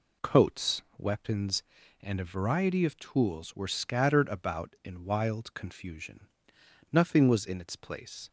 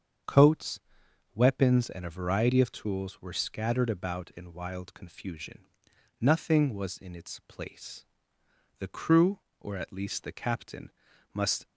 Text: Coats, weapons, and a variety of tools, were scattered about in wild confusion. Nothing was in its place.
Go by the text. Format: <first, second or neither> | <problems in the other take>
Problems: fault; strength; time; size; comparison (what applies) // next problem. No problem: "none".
first | starts louder than the rest; strong; until 1.8 s; 7.5 dB // goes on to say "The crew or at least the captain must"; strong; from 8.7 s on; 2.8 s long